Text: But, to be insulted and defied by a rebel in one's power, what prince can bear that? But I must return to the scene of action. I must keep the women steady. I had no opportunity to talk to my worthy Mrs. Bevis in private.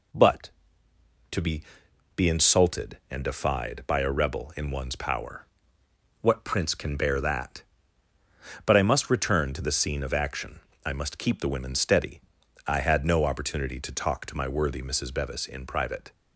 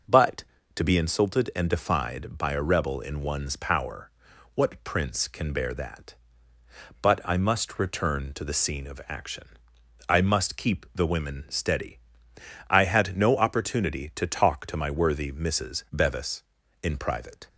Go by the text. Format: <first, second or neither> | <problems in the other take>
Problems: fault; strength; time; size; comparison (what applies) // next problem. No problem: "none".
second | says "be" twice; at 2.1 s